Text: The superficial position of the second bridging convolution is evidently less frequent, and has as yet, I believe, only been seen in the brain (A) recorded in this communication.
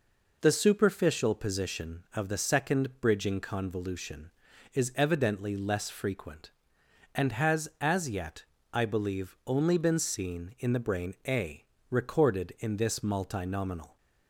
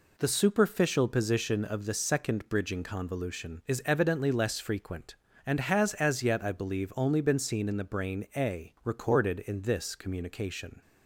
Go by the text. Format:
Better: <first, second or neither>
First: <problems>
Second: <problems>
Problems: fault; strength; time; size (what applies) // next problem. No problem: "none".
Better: second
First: says "multinominal" for "communication"; at 12.9 s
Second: none